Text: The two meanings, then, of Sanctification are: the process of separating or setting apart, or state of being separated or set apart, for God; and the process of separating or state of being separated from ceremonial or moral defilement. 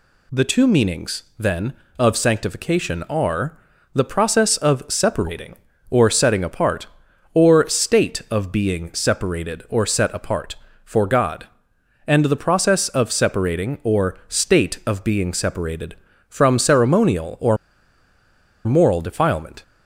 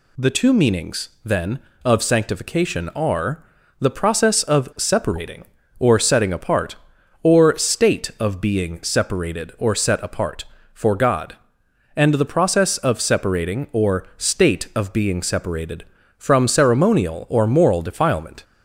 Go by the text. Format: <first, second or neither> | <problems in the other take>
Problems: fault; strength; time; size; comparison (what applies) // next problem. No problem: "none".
second | pauses between "or" and "moral"; at 17.5 s; 1.1 s long